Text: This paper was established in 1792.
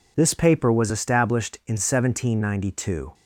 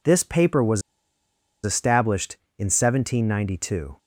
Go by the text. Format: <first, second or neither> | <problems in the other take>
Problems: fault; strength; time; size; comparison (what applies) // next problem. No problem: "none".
first | pauses between "was" and "established"; noticeable; at 0.8 s; 0.82 s long